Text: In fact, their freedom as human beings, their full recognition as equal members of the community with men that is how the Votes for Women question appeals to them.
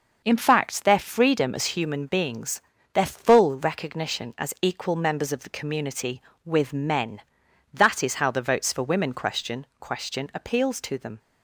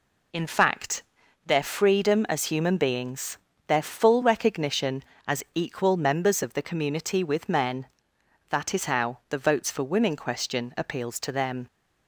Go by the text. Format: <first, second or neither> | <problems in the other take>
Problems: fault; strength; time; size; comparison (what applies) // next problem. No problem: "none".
second | says "question" twice; at 9.8 s